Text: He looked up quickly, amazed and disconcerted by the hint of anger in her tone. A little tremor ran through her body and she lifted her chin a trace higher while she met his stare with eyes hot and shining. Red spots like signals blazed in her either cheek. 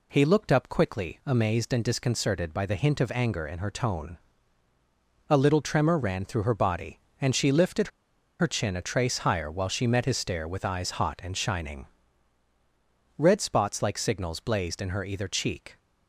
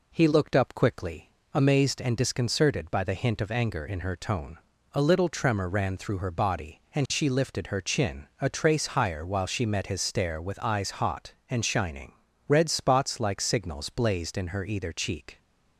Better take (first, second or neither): second